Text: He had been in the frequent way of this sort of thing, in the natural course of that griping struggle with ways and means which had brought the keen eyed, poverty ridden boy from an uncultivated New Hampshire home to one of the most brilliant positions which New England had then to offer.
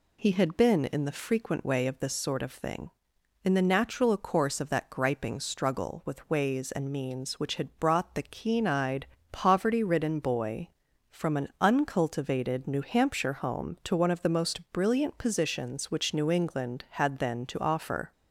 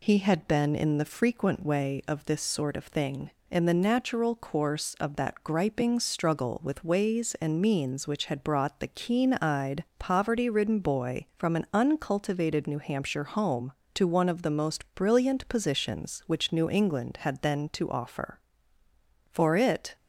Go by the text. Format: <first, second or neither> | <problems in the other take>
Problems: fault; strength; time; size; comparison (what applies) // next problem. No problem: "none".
first | goes on to say "For it"; noticeable; from 19.3 s on; 0.64 s long